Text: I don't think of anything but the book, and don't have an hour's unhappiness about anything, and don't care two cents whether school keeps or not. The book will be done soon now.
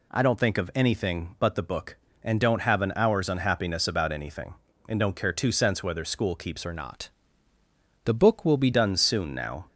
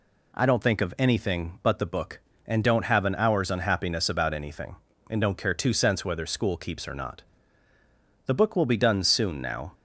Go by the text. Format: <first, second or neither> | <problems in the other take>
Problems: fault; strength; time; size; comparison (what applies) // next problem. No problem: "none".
second | changes voice from "or" to "be"; from 6.6 to 8.7 s; 2.1 s long